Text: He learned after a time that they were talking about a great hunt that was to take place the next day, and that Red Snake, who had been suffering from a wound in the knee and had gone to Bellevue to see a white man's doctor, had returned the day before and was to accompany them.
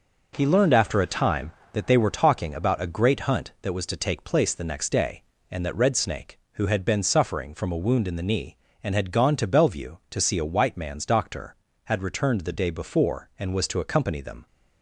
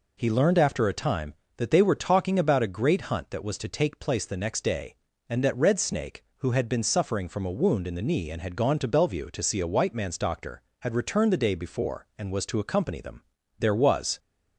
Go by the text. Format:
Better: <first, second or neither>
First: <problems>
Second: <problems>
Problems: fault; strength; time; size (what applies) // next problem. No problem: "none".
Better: first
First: none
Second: goes on to say "There was"; from 13.6 s on; 0.58 s long